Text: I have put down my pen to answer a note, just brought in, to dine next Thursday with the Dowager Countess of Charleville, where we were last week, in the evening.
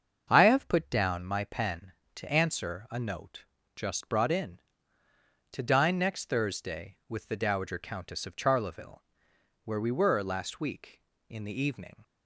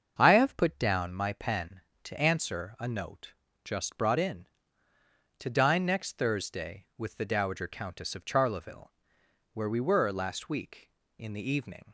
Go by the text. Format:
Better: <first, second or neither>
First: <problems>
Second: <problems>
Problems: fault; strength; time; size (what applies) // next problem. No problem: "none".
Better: neither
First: starts louder than the rest; until 1.3 s; 6.5 dB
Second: starts louder than the rest; until 1.2 s; 6.5 dB